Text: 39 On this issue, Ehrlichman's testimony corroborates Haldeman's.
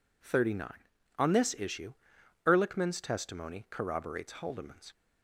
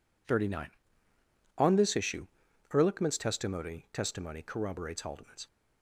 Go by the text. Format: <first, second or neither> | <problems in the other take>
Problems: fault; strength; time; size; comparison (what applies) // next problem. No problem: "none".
first | says "testimony" twice; at 3.9 s